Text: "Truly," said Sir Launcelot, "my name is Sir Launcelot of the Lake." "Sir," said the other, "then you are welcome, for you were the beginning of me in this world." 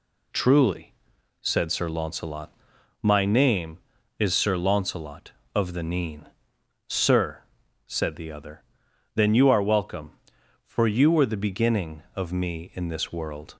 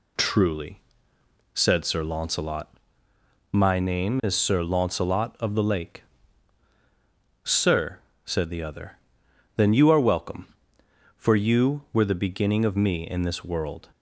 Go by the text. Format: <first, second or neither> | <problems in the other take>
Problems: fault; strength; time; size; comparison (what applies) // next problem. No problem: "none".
second | says "Neen" for "Lake"; at 5.8 s